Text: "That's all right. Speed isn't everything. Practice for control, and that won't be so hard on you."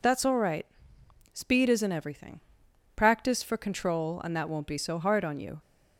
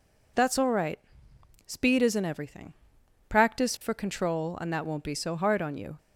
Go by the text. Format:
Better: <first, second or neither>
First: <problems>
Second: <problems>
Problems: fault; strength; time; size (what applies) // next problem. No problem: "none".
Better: neither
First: none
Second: none